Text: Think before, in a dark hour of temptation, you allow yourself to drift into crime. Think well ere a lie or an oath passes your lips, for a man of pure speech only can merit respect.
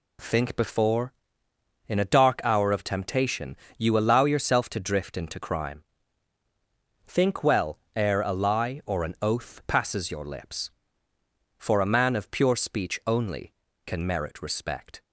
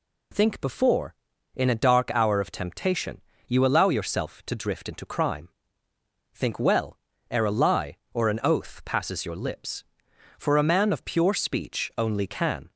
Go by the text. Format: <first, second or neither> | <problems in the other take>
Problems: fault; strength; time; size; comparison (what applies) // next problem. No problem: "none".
first | pauses between "well" and "ere"; slight; at 6.9 s; 0.34 s long; slight in the first // stops before "merit respect"; at 12.7 s